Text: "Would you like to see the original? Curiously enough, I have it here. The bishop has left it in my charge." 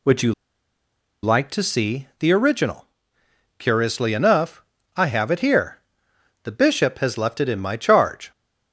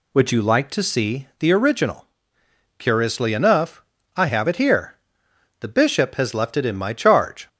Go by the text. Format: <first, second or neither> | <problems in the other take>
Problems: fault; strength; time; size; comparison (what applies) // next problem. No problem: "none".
second | pauses between "you" and "like"; noticeable; at 0.3 s; 0.90 s long